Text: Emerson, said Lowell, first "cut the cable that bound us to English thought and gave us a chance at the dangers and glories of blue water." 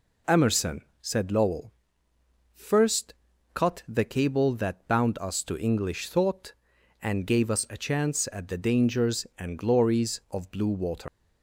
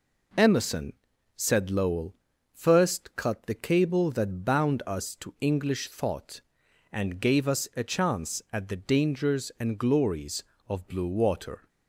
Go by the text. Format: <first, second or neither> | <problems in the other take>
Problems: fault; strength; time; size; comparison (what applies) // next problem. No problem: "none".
second | pauses between "first" and "cut"; at 3.1 s; 0.40 s long // leaves "water" unfinished; at 11.0 s; 125 ms